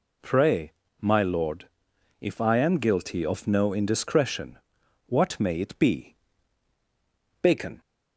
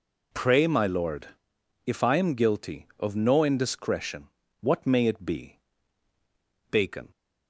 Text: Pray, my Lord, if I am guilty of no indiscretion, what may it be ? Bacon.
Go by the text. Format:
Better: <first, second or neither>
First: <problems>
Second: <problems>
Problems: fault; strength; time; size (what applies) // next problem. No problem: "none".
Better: neither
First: none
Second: none